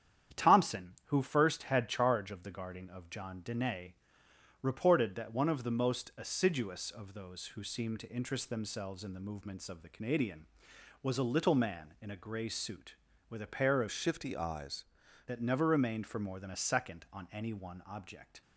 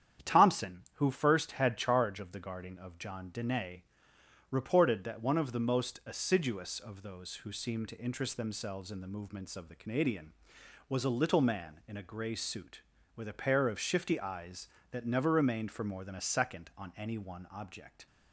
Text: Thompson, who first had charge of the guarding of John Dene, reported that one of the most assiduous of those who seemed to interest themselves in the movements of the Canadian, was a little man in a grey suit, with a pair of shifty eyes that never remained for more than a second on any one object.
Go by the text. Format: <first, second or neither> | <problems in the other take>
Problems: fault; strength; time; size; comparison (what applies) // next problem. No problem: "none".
second | starts louder than the rest; strong; until 1.4 s; 9.5 dB; strong in the second // changes voice from "shifty" to "eyes"; from 13.9 to 14.8 s; 0.9 s long